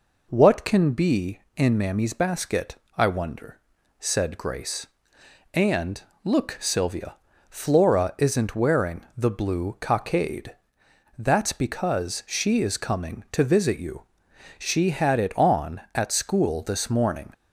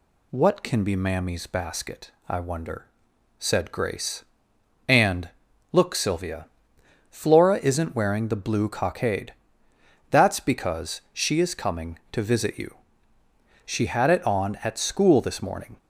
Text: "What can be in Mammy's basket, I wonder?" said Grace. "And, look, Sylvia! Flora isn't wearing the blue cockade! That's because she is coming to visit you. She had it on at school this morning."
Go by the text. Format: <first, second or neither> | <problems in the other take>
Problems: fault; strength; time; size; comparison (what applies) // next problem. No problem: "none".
first | skips "in"; at 0.9 s